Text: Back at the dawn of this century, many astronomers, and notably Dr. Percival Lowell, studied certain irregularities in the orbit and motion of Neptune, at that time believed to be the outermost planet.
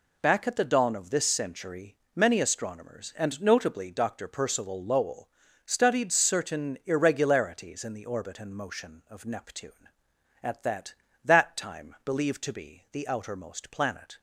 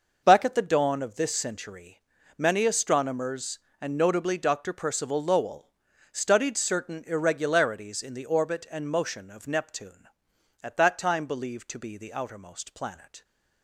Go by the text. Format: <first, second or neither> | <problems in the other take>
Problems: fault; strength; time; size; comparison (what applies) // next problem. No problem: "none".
second | says "that" twice; at 11.2 s